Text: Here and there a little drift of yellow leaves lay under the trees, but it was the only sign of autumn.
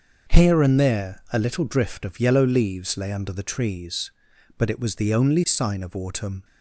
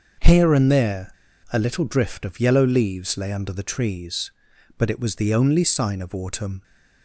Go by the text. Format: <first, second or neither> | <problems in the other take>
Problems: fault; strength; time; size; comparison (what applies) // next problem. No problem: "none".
first | pauses between "there" and "a"; at 1.1 s; 0.38 s long